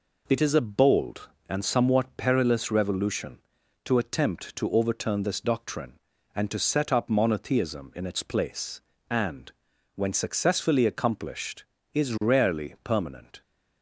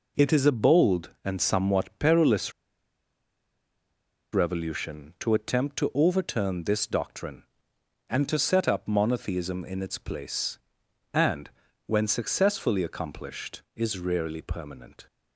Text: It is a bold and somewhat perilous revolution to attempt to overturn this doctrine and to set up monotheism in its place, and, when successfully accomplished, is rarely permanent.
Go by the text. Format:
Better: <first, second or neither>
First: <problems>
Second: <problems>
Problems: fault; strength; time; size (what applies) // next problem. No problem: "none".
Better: first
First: none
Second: pauses between "perilous" and "revolution"; strong; at 2.5 s; 1.8 s long